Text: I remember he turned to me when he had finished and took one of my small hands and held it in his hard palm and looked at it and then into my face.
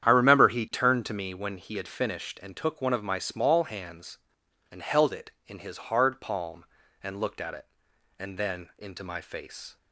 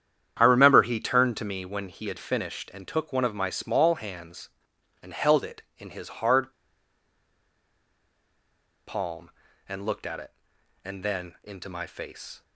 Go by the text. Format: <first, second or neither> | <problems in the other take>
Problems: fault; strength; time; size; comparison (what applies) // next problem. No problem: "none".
first | starts louder than the rest; strong; until 1.4 s; 9.5 dB; strong in the first // pauses between "hard" and "palm"; strong; at 6.5 s; 2.3 s long